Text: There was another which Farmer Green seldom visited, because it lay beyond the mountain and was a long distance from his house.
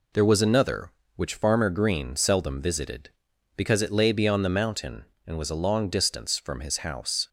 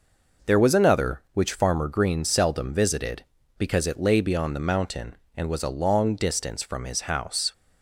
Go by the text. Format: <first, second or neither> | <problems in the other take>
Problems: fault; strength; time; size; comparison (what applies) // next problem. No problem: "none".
neither | none